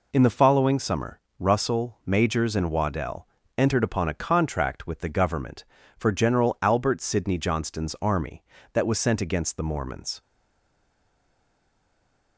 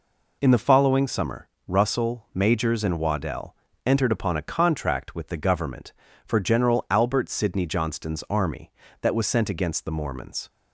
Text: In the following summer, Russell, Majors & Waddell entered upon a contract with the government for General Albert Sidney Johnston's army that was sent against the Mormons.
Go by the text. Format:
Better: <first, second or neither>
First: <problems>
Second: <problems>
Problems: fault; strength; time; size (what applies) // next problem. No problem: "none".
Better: second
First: pauses between "Waddell" and "entered"; slight; at 3.2 s; 0.30 s long // stays silent after the last word; from 10.2 s on; 2.1 s long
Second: pauses between "Waddell" and "entered"; slight; at 3.5 s; 0.30 s long